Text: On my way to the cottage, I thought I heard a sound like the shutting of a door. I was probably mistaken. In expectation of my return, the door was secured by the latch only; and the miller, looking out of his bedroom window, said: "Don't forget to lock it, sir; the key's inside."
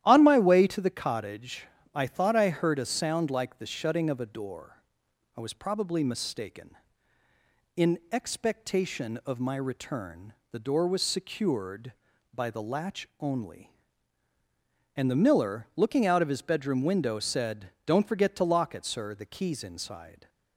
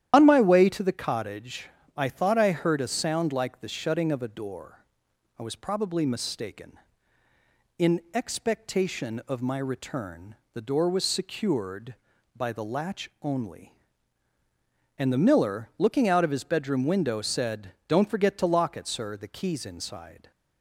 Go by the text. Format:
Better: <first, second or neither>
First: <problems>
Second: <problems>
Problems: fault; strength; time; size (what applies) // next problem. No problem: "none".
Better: first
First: starts louder than the rest; strong; until 1.0 s; 12 dB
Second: loses the start of "On"; at 0.1 s; 90 ms // starts louder than the rest; strong; until 1.1 s; 11 dB